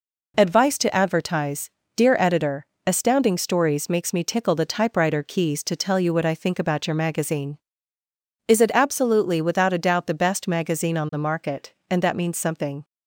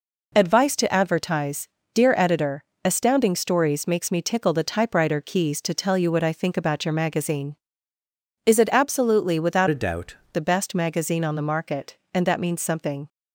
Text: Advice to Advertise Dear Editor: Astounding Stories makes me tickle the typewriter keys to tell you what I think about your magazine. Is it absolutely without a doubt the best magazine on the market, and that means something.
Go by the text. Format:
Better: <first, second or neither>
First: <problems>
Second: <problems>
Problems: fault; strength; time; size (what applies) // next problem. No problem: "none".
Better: first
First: pauses between "Advertise" and "Dear"; slight; at 1.6 s; 0.26 s long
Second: pauses between "Advertise" and "Dear"; slight; at 1.6 s; 0.26 s long // changes voice from "a" to "doubt"; from 9.7 to 10.1 s; 0.4 s long